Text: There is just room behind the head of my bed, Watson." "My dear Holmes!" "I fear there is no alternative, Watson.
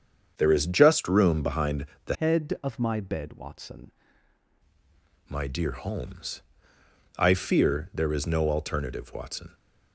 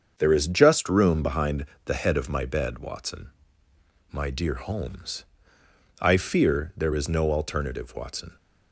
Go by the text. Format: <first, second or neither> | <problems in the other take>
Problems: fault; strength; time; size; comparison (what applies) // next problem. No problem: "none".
second | starts louder than the rest; strong; until 1.3 s; 7.5 dB; also in the second // pauses between "behind" and "the"; slight; at 1.8 s; 0.20 s long; slight in the second // changes voice from "head" to "Watson"; from 2.1 to 3.8 s; 1.7 s long